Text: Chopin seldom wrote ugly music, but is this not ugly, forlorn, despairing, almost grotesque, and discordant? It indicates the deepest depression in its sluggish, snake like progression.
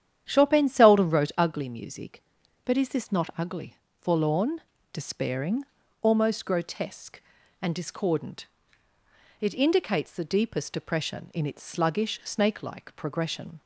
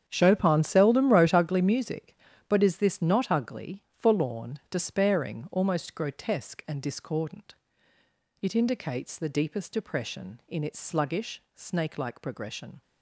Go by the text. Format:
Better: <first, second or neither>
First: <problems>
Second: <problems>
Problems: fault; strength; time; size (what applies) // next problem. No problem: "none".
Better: first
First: starts louder than the rest; strong; until 1.2 s; 9.5 dB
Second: gets quieter; strong; throughout; 13 dB // starts louder than the rest; strong; until 1.0 s; 8.5 dB